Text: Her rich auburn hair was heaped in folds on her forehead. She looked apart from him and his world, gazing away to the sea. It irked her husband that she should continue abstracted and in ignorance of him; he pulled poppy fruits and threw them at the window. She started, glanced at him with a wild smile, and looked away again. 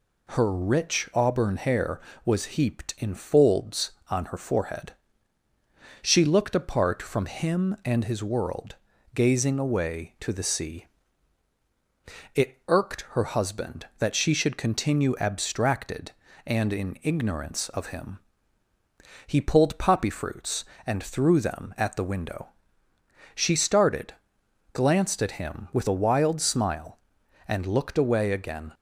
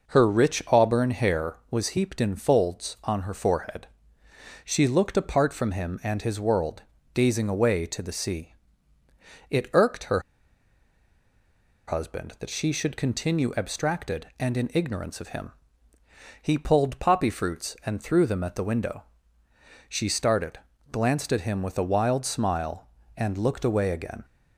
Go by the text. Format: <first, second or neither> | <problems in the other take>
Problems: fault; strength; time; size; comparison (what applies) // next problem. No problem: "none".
first | pauses between "her" and "husband"; strong; at 10.1 s; 1.6 s long